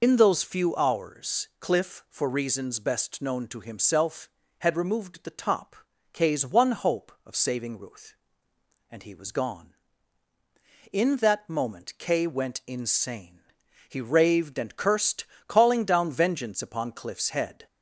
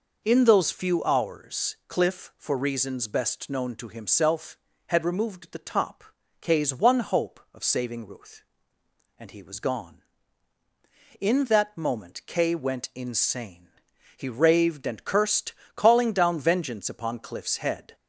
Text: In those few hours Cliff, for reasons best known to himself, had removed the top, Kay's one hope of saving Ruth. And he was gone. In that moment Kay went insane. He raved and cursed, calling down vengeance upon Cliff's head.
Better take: second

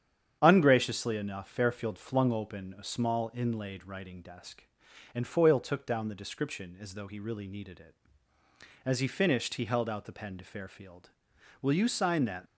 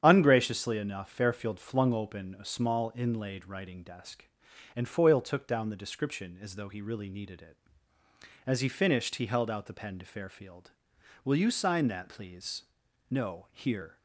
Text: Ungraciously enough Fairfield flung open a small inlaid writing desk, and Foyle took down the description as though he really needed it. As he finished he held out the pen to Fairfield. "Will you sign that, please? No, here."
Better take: second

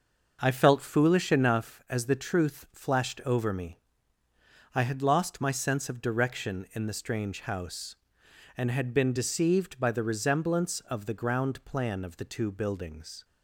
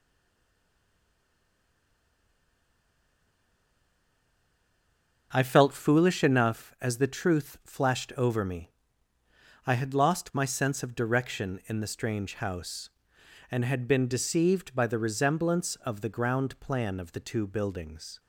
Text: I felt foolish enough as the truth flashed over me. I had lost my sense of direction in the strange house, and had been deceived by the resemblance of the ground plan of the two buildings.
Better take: first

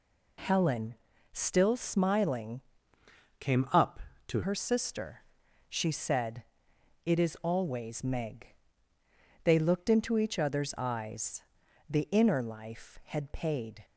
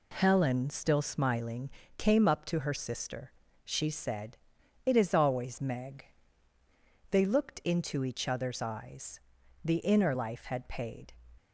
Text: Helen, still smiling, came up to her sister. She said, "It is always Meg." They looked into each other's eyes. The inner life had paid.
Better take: second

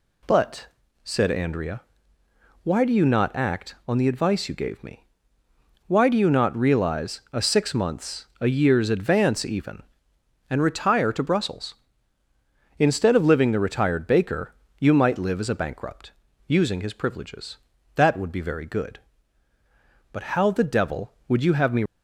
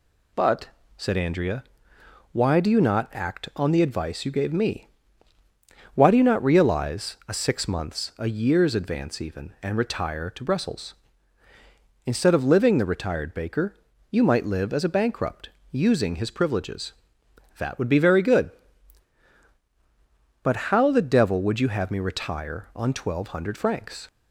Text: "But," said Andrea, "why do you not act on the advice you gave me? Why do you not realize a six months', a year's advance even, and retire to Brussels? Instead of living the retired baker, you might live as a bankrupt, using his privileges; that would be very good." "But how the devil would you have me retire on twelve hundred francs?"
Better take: second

